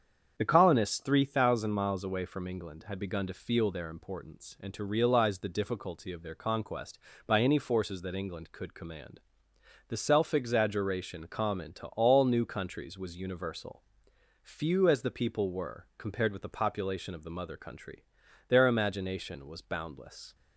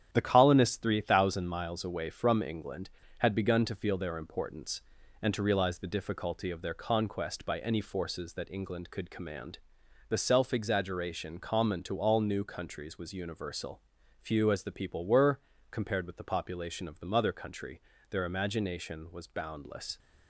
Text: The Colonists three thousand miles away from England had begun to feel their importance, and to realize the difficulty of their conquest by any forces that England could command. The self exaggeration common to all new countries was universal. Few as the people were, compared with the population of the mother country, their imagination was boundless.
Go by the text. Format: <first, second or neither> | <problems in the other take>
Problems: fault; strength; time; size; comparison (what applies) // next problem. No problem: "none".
first | gets quieter; throughout; 6.5 dB // starts louder than the rest; strong; until 1.1 s; 10 dB; strong in the first